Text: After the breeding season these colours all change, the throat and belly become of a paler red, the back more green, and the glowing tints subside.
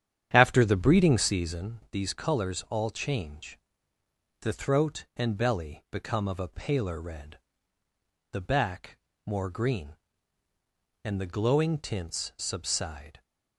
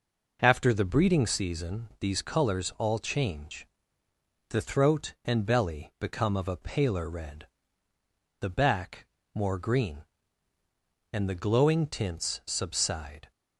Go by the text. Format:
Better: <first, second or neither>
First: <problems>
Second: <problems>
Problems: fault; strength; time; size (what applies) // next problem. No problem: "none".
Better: second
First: starts louder than the rest; strong; until 1.7 s; 9.5 dB // pauses between "back" and "more"; slight; at 8.9 s; 0.30 s long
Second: pauses between "back" and "more"; slight; at 9.0 s; 0.30 s long